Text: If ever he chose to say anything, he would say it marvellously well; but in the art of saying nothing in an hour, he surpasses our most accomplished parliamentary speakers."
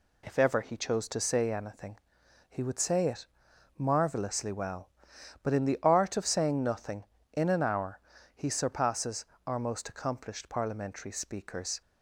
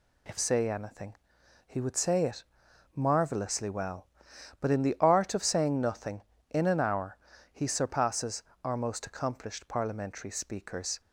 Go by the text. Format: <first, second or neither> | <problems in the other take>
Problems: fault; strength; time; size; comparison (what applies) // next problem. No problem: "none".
first | skips "ever he chose to"; at 0.3 s // pauses between "it" and "marvellously"; noticeable; at 2.4 s; 0.52 s long; noticeable in the first // pauses between "surpasses" and "our"; slight; at 8.4 s; 0.20 s long; slight in the first